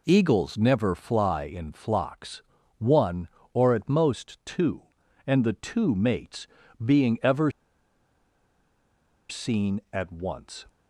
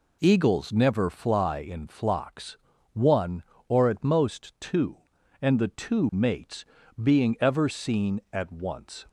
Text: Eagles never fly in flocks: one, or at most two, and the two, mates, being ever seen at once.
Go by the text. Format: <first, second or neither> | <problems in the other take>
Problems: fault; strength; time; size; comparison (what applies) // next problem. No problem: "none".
second | pauses between "ever" and "seen"; strong; at 7.4 s; 1.7 s long